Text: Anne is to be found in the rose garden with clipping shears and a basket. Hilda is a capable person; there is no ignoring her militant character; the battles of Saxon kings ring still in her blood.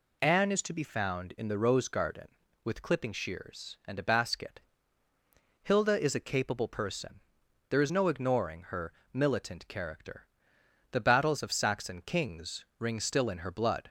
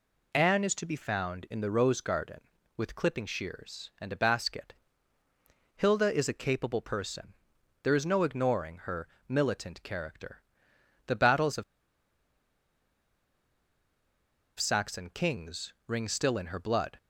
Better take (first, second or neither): first